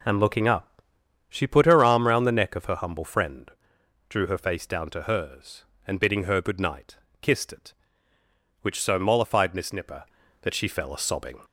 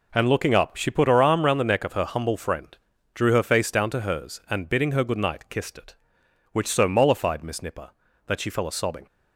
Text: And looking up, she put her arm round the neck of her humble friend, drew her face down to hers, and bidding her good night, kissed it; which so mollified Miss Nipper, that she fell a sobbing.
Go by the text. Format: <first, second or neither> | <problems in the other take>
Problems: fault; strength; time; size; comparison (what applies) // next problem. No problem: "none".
neither | none